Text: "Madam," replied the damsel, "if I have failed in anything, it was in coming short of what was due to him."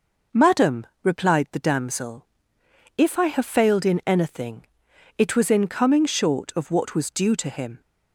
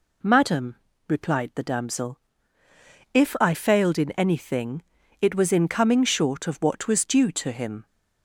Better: first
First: none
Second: skips "have"; at 3.5 s

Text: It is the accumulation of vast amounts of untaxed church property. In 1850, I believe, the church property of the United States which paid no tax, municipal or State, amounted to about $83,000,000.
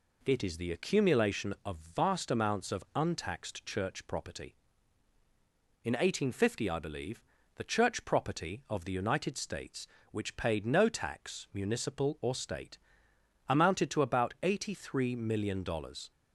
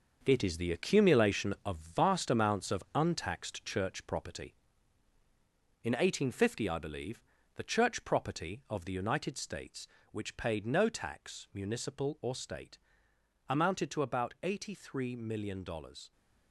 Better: first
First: none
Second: gets quieter; strong; throughout; 8 dB

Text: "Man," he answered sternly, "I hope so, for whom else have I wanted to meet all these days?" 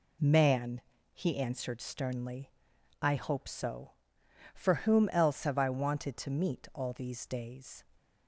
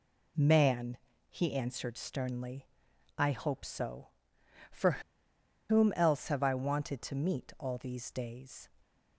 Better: first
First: none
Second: pauses between "for" and "whom"; noticeable; at 4.9 s; 0.69 s long

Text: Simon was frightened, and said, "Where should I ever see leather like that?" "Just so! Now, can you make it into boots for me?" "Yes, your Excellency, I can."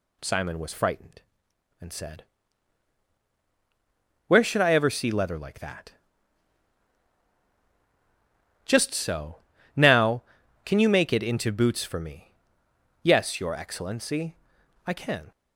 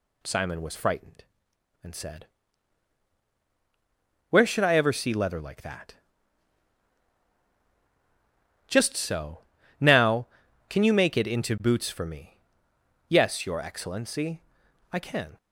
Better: neither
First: none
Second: none

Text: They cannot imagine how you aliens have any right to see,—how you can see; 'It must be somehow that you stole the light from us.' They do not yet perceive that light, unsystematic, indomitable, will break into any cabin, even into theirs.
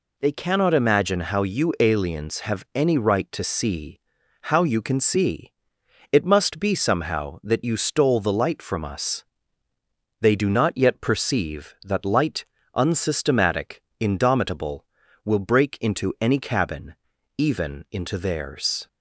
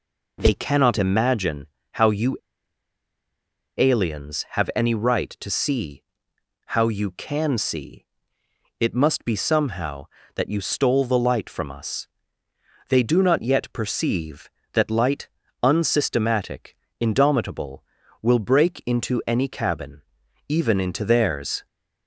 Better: first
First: none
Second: pauses between "imagine" and "how"; slight; at 1.6 s; 0.26 s long // pauses between "you" and "aliens"; strong; at 2.3 s; 1.3 s long

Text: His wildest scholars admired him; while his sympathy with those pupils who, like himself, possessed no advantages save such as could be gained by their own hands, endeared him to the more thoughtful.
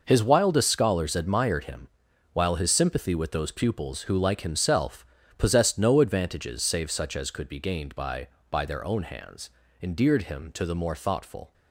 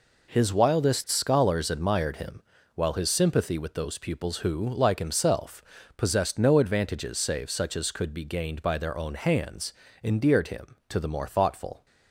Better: second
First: says "by" twice; at 8.4 s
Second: none

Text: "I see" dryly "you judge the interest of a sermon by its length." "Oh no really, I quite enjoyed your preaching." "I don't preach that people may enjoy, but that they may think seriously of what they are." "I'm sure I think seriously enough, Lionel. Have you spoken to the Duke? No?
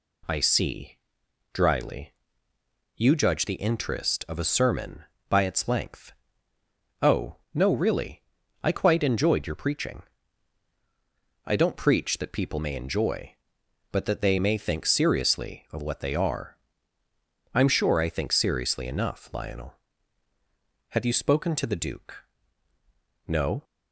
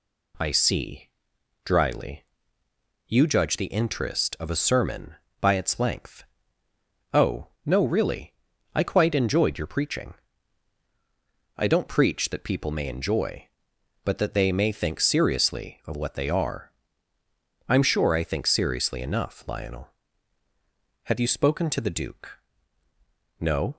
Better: neither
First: pauses between "see" and "dryly"; noticeable; at 0.9 s; 0.56 s long // pauses between "dryly" and "you"; noticeable; at 2.1 s; 0.82 s long // pauses between "Oh" and "no"; slight; at 7.3 s; 0.16 s long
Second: pauses between "see" and "dryly"; noticeable; at 1.0 s; 0.56 s long // pauses between "dryly" and "you"; noticeable; at 2.2 s; 0.82 s long // pauses between "Oh" and "no"; slight; at 7.4 s; 0.16 s long

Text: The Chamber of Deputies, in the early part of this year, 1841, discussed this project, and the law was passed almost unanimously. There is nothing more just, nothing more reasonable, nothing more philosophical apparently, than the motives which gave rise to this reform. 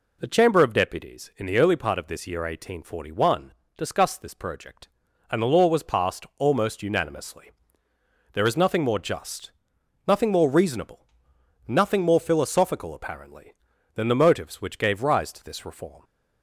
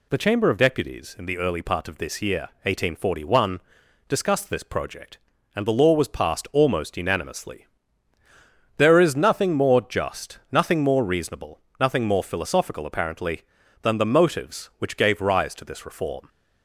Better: neither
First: none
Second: none

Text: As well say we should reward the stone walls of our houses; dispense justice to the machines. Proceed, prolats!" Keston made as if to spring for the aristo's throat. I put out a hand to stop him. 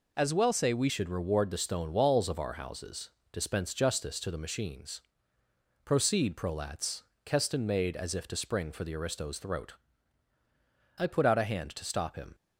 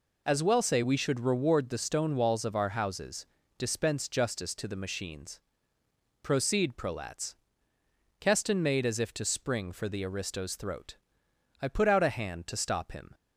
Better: second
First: changes voice at "should"; from 0.8 s on; 11.5 s long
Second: none

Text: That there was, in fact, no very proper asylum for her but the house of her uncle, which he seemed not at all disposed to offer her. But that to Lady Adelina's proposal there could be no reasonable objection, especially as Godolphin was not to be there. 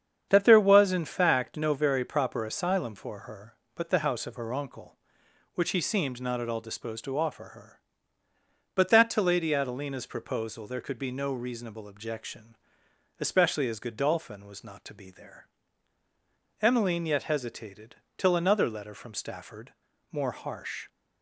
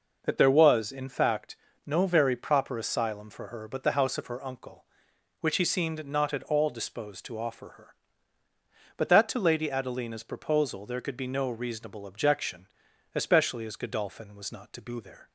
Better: second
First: starts louder than the rest; strong; until 1.3 s; 8 dB // goes on to say "Emmeline yet hesitated till another letter from Stafford more harsh"; strong; from 16.6 s on; 4.2 s long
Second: none

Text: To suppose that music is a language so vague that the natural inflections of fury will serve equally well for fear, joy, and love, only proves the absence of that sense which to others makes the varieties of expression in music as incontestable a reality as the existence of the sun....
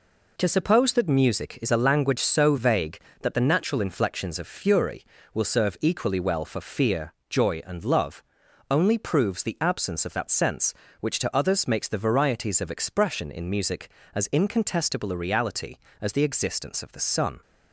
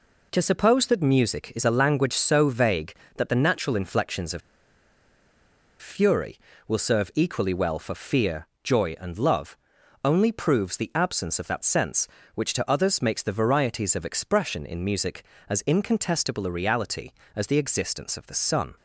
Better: first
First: none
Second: pauses between "of" and "fury"; strong; at 4.4 s; 1.4 s long

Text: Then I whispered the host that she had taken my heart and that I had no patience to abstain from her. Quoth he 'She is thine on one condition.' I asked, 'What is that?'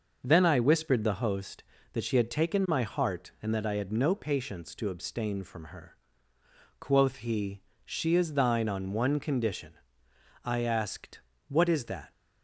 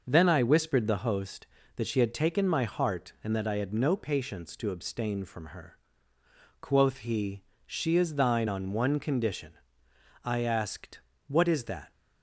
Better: neither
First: pauses between "he" and "She"; slight; at 7.6 s; 0.22 s long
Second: pauses between "he" and "She"; slight; at 7.4 s; 0.22 s long

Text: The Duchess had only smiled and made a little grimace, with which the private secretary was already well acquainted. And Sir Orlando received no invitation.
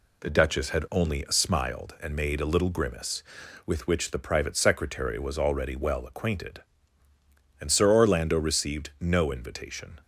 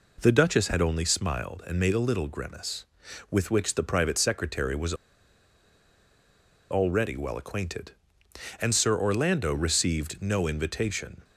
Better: first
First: none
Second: pauses between "was" and "already"; strong; at 4.9 s; 1.7 s long

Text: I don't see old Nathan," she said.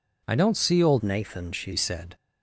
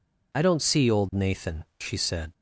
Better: second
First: changes voice from "Nathan" to "she"; from 1.0 to 1.7 s; 0.7 s long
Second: none

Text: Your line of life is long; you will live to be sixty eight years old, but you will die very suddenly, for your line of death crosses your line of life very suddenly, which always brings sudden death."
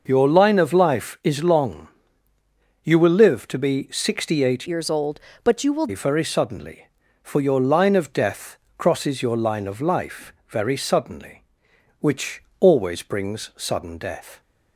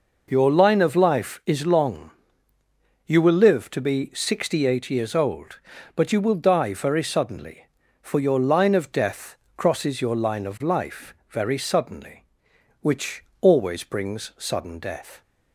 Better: second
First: changes voice from "years" to "will"; from 4.6 to 5.8 s; 1.2 s long // pauses between "death" and "crosses"; slight; at 8.5 s; 0.20 s long // pauses between "life" and "very"; slight; at 10.3 s; 0.16 s long // pauses between "which" and "always"; slight; at 12.4 s; 0.16 s long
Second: pauses between "death" and "crosses"; slight; at 9.3 s; 0.20 s long // pauses between "life" and "very"; slight; at 11.1 s; 0.16 s long // pauses between "which" and "always"; slight; at 13.2 s; 0.16 s long

